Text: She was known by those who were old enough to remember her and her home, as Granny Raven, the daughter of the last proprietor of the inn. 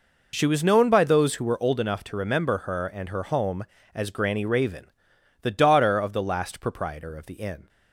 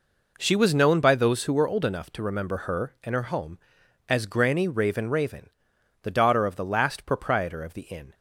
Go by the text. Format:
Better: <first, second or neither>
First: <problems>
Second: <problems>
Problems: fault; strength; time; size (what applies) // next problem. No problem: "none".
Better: first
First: none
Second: says "Raven" twice; at 5.0 s